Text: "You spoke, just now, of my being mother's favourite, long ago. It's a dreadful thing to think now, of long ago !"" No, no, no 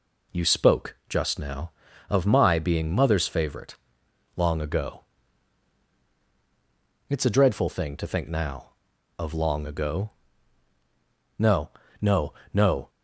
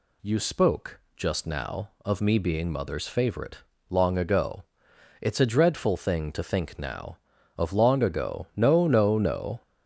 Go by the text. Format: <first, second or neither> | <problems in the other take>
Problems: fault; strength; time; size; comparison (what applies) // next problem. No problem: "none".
first | says "me" for "my"; at 2.1 s